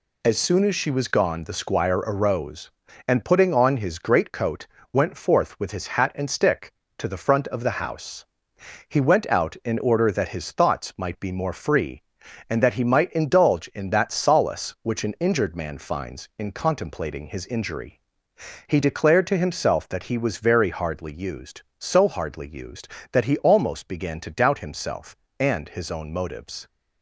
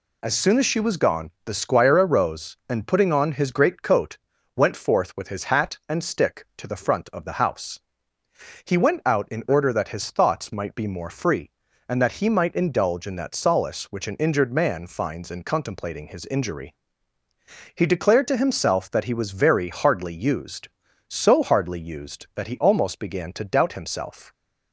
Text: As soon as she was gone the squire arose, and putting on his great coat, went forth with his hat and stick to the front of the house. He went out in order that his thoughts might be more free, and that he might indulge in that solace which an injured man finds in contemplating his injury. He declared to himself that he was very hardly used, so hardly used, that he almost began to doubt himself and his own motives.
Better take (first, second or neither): first